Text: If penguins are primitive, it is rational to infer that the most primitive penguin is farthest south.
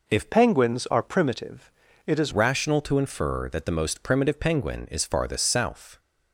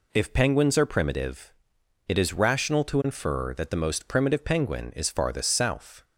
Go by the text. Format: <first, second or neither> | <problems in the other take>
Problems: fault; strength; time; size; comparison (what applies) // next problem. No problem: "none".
second | changes voice from "penguins" to "is"; from 0.3 to 2.3 s; 2.0 s long